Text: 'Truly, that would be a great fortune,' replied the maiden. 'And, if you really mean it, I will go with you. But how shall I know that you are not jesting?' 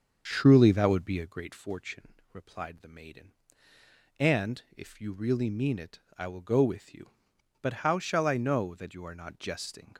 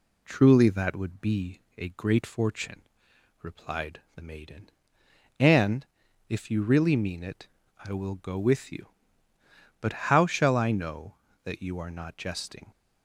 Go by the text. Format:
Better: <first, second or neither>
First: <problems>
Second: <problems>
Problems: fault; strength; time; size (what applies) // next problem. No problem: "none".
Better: second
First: starts louder than the rest; until 1.4 s; 6.5 dB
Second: none